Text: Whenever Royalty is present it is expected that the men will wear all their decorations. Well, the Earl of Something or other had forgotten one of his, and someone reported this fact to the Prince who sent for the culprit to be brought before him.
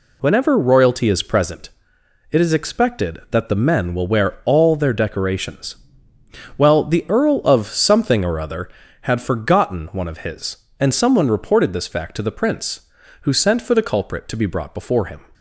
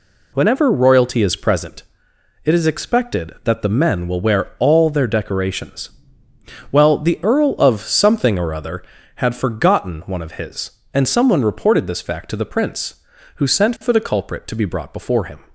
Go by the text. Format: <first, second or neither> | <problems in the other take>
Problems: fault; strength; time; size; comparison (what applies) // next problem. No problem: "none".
neither | pauses between "present" and "it"; noticeable; the same in both